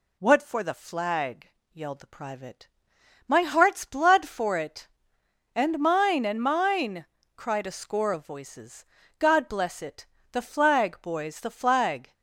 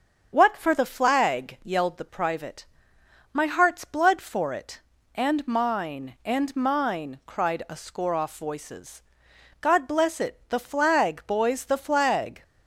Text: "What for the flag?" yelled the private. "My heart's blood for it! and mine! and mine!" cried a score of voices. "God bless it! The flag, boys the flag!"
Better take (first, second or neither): first